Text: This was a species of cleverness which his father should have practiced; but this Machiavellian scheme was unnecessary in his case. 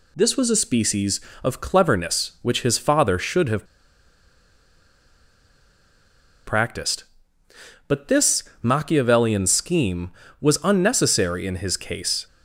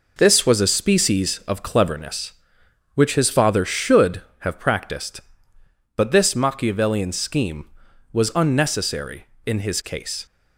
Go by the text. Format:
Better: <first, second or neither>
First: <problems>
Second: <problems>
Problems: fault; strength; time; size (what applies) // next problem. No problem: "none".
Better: second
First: pauses between "have" and "practiced"; strong; at 3.6 s; 2.8 s long // pauses between "this" and "Machiavellian"; slight; at 8.4 s; 0.20 s long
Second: none